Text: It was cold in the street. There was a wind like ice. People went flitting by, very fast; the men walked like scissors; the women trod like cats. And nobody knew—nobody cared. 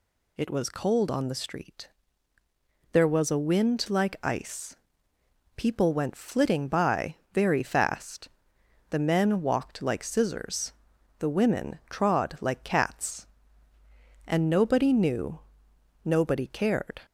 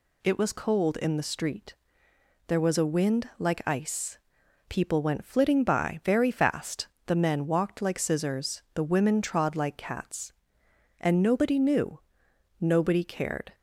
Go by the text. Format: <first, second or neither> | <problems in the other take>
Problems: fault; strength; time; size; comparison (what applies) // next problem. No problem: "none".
second | says "on" for "in"; at 1.0 s